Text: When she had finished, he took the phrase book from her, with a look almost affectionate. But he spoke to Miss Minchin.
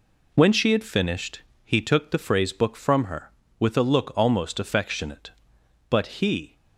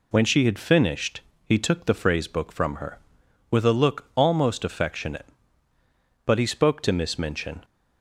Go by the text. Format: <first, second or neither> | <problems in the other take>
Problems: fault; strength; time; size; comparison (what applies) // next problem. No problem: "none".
second | stops before "spoke to Miss Minchin"; at 6.5 s